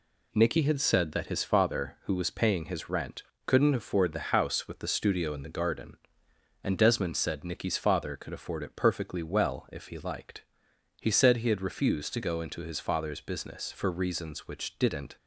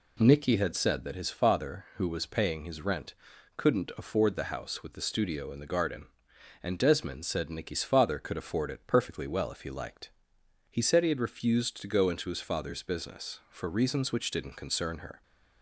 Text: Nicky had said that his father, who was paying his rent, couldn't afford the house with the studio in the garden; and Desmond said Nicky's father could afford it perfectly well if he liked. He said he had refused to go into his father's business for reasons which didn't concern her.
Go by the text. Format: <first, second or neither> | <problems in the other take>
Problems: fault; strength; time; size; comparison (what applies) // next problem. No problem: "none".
second | stops before "concern her"; at 15.1 s